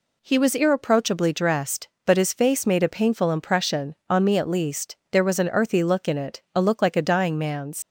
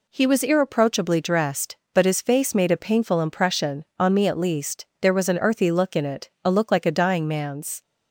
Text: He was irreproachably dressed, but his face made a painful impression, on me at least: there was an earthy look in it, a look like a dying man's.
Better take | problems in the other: second | leaves "man's" unfinished; at 7.8 s; 95 ms

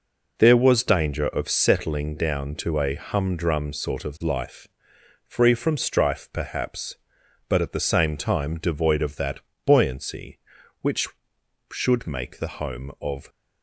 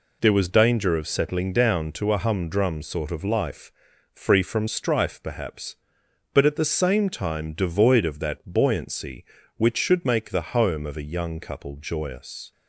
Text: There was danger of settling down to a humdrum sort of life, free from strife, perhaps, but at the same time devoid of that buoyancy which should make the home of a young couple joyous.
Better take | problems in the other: second | pauses between "that" and "buoyancy"; slight; at 9.4 s; 0.24 s long // stops before "a young couple joyous"; at 13.2 s

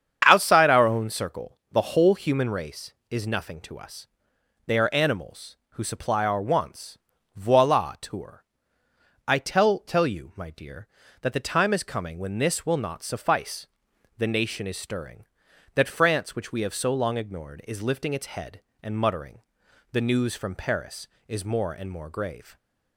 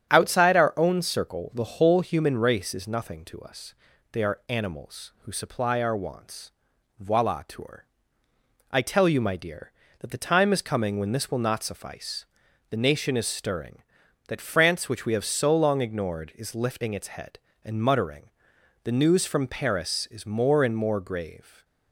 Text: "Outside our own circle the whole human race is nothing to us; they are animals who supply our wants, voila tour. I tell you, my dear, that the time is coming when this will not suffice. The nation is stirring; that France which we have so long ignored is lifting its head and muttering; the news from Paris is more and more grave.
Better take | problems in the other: second | starts louder than the rest; strong; until 1.2 s; 8 dB; strong in the second // says "tell" twice; at 9.7 s

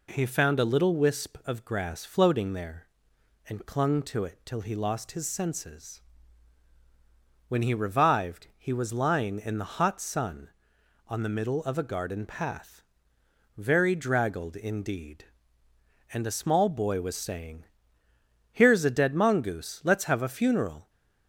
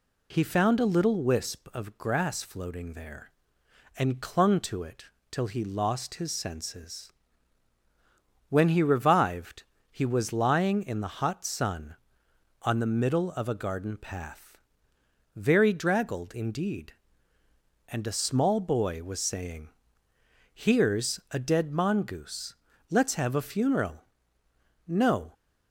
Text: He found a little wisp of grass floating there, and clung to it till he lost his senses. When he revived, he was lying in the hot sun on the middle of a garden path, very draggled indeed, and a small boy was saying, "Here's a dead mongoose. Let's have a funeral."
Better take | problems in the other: first | pauses between "it" and "till"; slight; at 5.0 s; 0.22 s long // goes on to say "No"; slight; from 24.8 s on; 0.46 s long

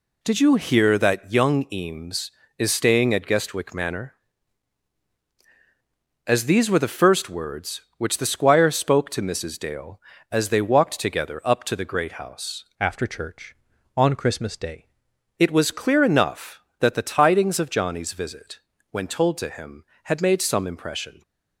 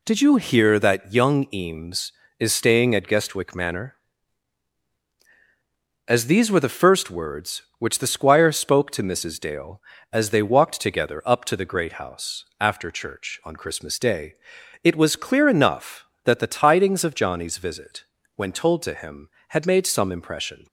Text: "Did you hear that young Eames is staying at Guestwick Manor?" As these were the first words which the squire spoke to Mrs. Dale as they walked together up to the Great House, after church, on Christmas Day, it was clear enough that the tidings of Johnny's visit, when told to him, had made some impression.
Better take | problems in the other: second | changes voice from "after" to "Day"; from 12.7 to 14.8 s; 2.1 s long

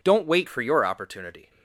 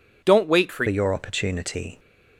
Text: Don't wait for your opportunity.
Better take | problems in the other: first | changes voice at "your"; from 0.8 s on; 1.1 s long

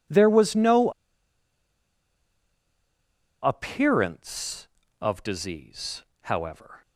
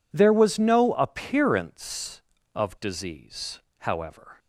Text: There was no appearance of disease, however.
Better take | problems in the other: second | pauses between "no" and "appearance"; strong; at 0.8 s; 2.5 s long

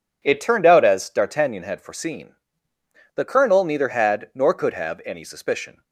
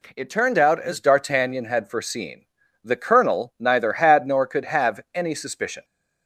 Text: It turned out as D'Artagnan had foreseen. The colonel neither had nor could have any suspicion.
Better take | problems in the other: neither | none

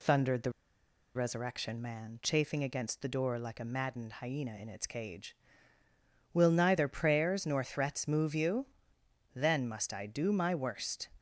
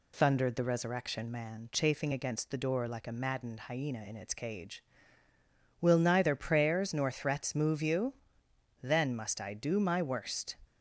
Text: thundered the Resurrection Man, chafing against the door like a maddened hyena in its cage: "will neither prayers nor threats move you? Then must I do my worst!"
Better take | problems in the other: second | pauses between "the" and "Resurrection"; noticeable; at 0.4 s; 0.65 s long

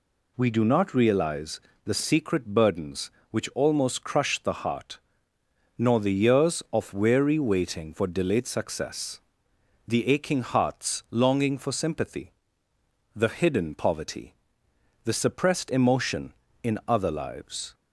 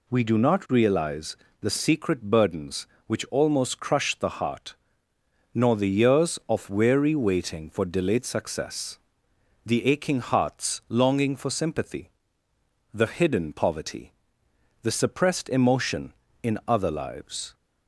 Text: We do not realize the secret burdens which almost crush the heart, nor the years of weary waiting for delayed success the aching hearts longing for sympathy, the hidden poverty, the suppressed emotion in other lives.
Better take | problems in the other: neither | pauses between "realize" and "the"; slight; the same in both // pauses between "success" and "the"; noticeable; the same in both

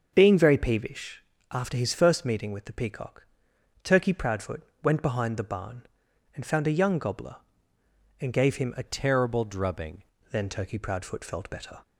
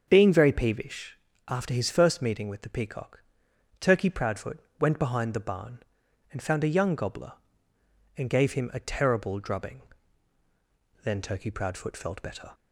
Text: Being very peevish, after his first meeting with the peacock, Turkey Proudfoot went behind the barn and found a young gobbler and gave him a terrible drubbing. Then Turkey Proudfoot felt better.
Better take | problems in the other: second | starts louder than the rest; until 1.1 s; 6.5 dB; also in the second // pauses between "Proudfoot" and "went"; slight; at 4.6 s; 0.22 s long; slight in the second // changes voice from "terrible" to "drubbing"; from 8.8 to 9.9 s; 1.1 s long

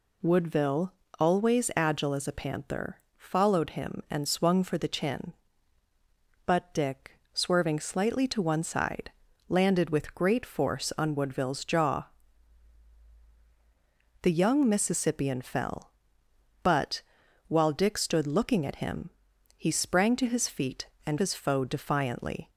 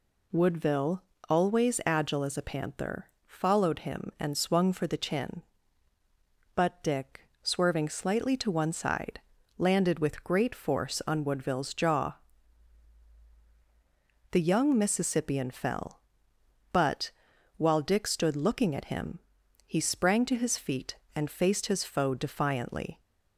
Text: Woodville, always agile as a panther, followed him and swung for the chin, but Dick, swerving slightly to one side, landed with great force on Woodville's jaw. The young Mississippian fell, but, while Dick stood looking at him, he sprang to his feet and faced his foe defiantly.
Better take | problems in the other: second | skips "faced"; at 21.1 s

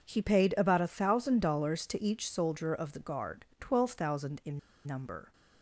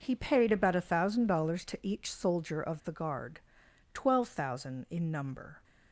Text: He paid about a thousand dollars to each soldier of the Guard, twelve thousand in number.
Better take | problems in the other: second | pauses between "in" and "number"; slight; at 4.5 s; 0.25 s long

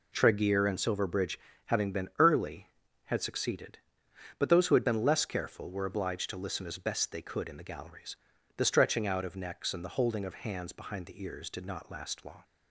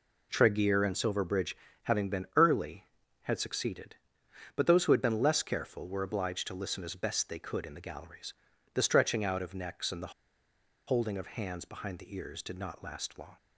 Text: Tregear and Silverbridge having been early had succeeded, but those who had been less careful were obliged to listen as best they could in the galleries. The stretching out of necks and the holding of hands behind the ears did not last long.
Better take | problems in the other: first | pauses between "Silverbridge" and "having"; slight; at 1.5 s; 0.26 s long; slight in the first // pauses between "the" and "holding"; noticeable; at 10.1 s; 0.75 s long

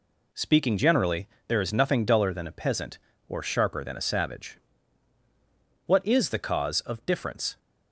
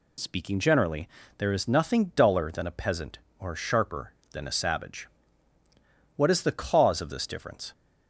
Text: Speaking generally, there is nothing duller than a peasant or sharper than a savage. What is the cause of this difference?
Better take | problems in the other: second | skips "this"; at 7.0 s

